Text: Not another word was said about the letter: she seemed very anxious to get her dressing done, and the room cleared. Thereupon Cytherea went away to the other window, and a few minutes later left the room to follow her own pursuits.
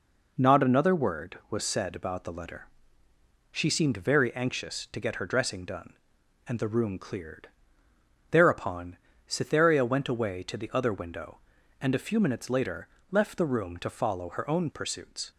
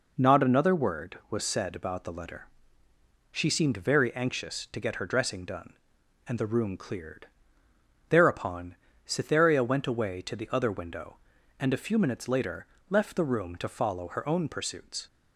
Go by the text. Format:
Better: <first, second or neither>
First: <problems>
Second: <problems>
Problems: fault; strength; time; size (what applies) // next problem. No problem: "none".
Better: neither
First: pauses between "Thereupon" and "Cytherea"; slight; at 8.9 s; 0.30 s long // pauses between "later" and "left"; slight; at 12.8 s; 0.22 s long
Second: pauses between "Thereupon" and "Cytherea"; slight; at 8.7 s; 0.30 s long // pauses between "later" and "left"; slight; at 12.6 s; 0.22 s long